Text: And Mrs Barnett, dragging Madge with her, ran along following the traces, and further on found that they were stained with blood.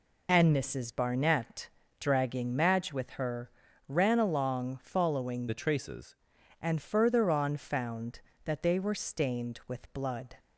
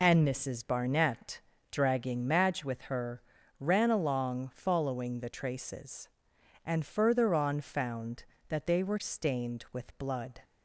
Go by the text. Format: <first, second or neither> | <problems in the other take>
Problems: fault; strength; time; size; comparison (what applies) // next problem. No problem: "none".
second | changes voice from "the" to "traces"; from 5.4 to 6.1 s; 0.7 s long